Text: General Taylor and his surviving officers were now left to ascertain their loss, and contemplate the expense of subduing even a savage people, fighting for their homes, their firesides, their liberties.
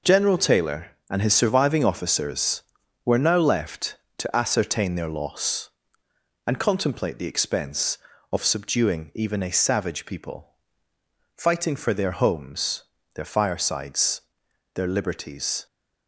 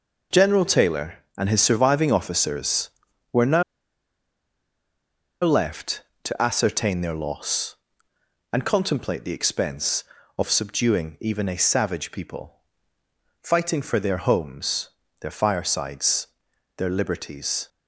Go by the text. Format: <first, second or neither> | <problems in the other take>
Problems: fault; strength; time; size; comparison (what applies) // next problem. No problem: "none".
first | pauses between "now" and "left"; strong; at 3.6 s; 1.8 s long